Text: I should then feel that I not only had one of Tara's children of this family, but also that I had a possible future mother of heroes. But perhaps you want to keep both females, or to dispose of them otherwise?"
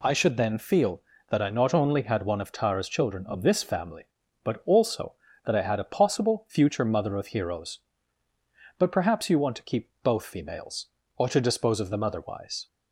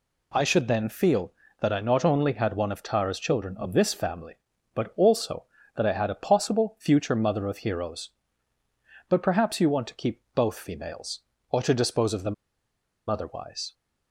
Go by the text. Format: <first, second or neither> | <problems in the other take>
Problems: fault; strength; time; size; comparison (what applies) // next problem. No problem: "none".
first | pauses between "them" and "otherwise"; noticeable; at 12.3 s; 0.74 s long